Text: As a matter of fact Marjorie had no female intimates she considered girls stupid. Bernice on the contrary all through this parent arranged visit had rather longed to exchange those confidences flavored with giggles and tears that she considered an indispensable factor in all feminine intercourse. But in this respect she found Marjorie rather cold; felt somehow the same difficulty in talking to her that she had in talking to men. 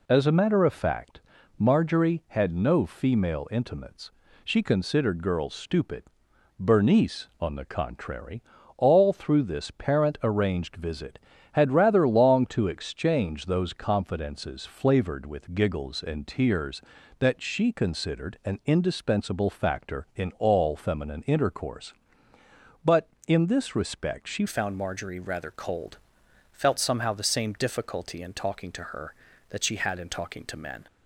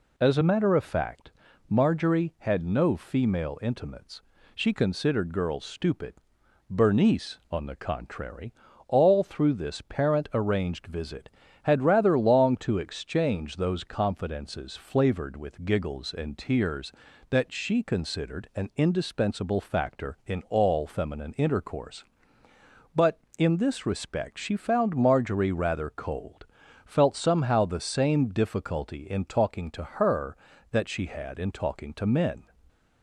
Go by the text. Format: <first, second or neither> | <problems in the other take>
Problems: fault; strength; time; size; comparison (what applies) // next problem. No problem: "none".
second | pauses between "fact" and "Marjorie"; at 1.1 s; 0.38 s long; also in the second // pauses between "intimates" and "she"; slight; at 4.1 s; 0.32 s long; slight in the second // pauses between "contrary" and "all"; slight; at 8.4 s; 0.34 s long; slight in the second // changes voice at "found"; from 24.4 s on; 6.4 s long